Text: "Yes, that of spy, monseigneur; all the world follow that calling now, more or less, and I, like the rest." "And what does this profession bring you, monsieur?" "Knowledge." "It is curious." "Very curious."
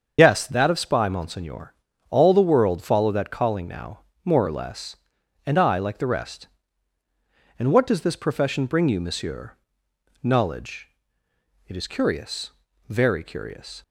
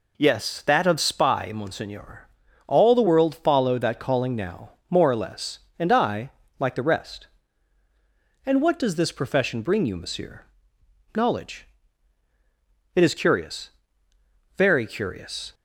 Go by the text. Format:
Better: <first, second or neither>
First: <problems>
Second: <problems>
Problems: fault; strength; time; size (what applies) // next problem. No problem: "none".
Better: second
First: loses the start of "Yes"; at 0.1 s; 90 ms // starts louder than the rest; until 1.2 s; 7 dB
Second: none